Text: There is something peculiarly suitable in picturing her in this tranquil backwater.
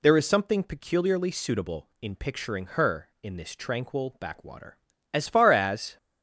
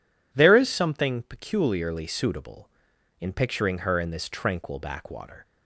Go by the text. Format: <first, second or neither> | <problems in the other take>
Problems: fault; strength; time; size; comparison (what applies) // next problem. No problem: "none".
second | goes on to say "As far as"; noticeable; from 5.1 s on; 0.86 s long